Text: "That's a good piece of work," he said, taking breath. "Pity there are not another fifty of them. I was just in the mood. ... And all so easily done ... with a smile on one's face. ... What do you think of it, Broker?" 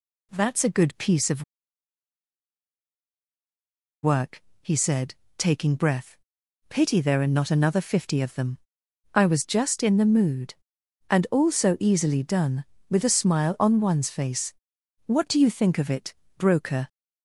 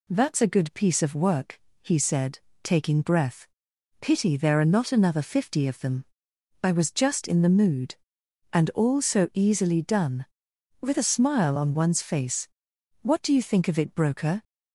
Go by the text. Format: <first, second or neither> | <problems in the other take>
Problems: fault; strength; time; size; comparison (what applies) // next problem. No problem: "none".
second | pauses between "of" and "work"; strong; at 1.4 s; 2.6 s long